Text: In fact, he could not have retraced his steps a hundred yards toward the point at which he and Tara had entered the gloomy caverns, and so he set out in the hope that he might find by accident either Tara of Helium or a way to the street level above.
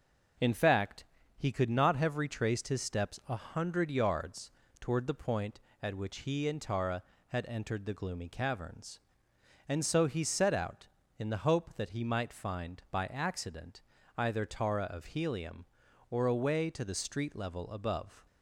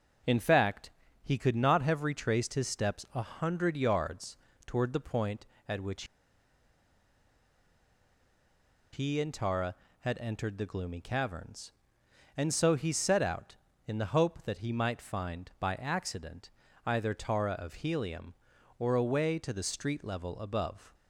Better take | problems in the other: first | pauses between "yards" and "toward"; slight; at 4.3 s; 0.30 s long; slight in the first // pauses between "which" and "he"; strong; at 6.0 s; 2.8 s long // pauses between "accident" and "either"; slight; at 16.4 s; 0.36 s long; slight in the first

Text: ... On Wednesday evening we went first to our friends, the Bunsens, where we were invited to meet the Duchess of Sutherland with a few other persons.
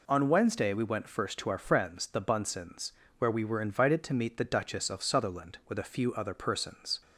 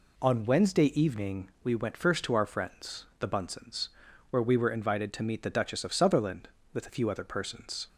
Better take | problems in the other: second | skips "evening"; at 0.7 s

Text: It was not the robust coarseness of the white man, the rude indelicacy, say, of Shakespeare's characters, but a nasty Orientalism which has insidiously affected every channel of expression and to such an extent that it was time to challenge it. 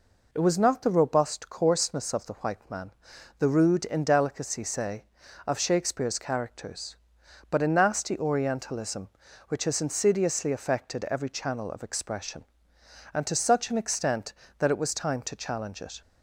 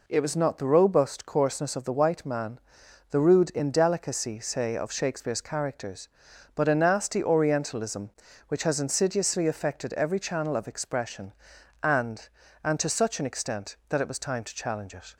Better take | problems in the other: first | says "and" twice; at 12.6 s

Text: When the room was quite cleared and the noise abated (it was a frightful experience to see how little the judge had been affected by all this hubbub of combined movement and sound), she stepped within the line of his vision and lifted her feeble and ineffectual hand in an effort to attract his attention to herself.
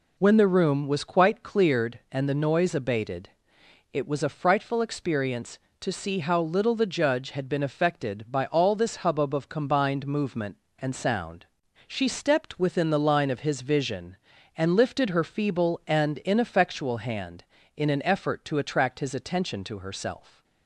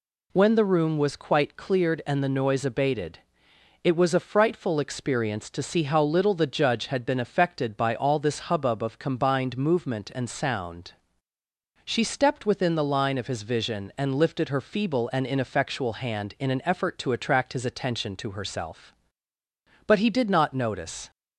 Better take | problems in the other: first | goes on to say "But he did not notice"; noticeable; from 19.8 s on; 1.2 s long

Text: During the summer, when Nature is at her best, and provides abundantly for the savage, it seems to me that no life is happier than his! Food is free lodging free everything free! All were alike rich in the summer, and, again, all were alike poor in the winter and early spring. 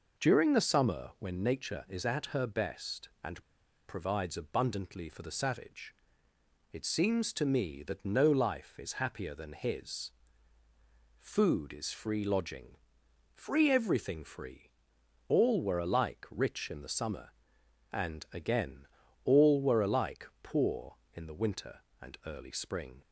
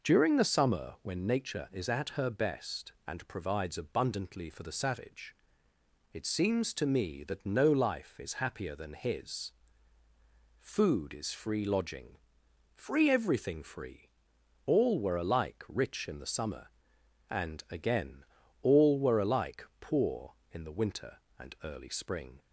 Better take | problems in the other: second | pauses between "and" and "provides"; at 3.4 s; 0.43 s long // pauses between "lodging" and "free"; noticeable; at 12.7 s; 0.58 s long; noticeable in the second

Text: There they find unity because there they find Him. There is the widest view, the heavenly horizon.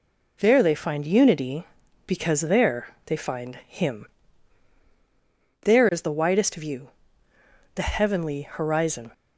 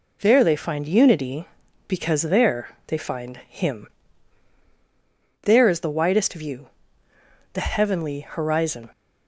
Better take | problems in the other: neither | pauses between "there" and "they"; slight; the same in both

